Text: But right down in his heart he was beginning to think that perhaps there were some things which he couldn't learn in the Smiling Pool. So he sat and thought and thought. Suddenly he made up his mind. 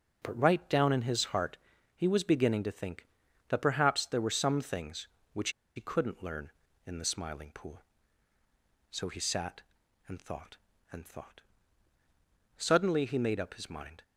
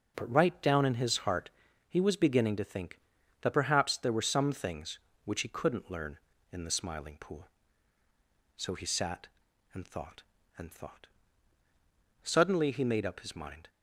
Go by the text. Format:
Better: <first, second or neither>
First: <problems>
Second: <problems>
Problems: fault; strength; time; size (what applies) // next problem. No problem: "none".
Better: second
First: pauses between "heart" and "he"; at 1.5 s; 0.38 s long // pauses between "which" and "he"; slight; at 5.5 s; 0.25 s long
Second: pauses between "heart" and "he"; at 1.4 s; 0.38 s long